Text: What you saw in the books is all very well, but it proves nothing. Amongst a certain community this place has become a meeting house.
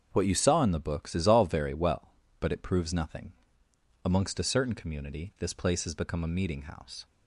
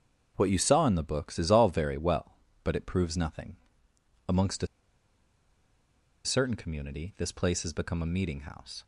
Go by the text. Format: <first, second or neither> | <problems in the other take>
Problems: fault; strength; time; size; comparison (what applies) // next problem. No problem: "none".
first | starts louder than the rest; strong; until 1.3 s; 7 dB; also in the first // pauses between "a" and "certain"; strong; at 4.6 s; 1.5 s long